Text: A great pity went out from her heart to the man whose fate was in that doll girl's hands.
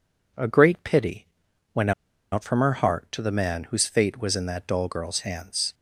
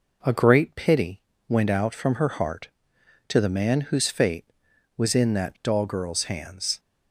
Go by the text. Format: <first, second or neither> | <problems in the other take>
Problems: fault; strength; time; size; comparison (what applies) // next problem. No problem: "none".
second | pauses between "pity" and "went"; noticeable; at 1.2 s; 0.48 s long; slight in the second // pauses between "went" and "out"; at 1.9 s; 0.40 s long